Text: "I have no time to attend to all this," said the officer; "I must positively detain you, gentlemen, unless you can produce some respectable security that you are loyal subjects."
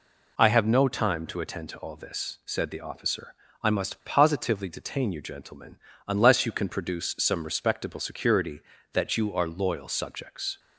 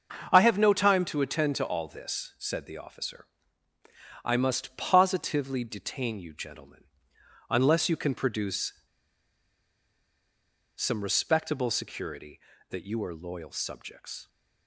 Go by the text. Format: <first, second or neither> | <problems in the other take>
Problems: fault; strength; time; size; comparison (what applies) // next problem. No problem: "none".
first | starts louder than the rest; until 1.3 s; 6.5 dB // pauses between "produce" and "some"; strong; at 8.7 s; 2.0 s long